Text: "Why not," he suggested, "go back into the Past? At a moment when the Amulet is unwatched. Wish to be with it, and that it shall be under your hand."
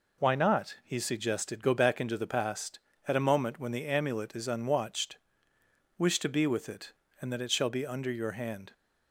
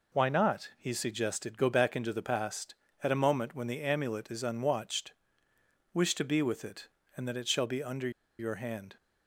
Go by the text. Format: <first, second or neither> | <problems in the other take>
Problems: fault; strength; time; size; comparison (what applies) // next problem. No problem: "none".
first | pauses between "under" and "your"; slight; at 8.0 s; 0.29 s long